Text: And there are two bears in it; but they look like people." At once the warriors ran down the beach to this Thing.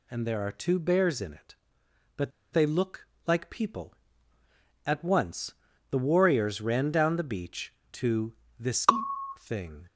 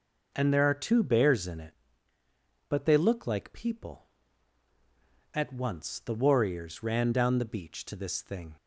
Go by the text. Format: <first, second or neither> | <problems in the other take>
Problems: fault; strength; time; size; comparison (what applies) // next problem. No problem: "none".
second | pauses between "but" and "they"; slight; at 2.3 s; 0.21 s long // pauses between "look" and "like"; slight; at 3.0 s; 0.20 s long // pauses between "once" and "the"; at 5.5 s; 0.38 s long // pauses between "to" and "this"; slight; at 8.3 s; 0.26 s long // pauses between "this" and "Thing"; noticeable; at 8.8 s; 0.54 s long